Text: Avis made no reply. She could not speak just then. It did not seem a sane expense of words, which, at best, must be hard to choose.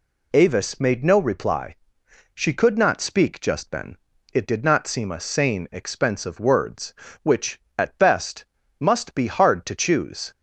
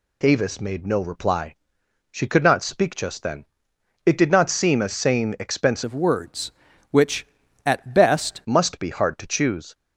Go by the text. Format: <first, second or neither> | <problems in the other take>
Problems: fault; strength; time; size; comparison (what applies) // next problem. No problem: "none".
first | changes voice from "of" to "best"; from 5.8 to 8.4 s; 2.6 s long